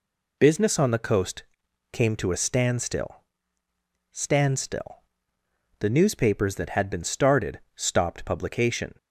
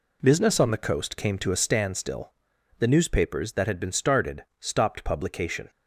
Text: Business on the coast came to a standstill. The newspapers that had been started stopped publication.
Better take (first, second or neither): second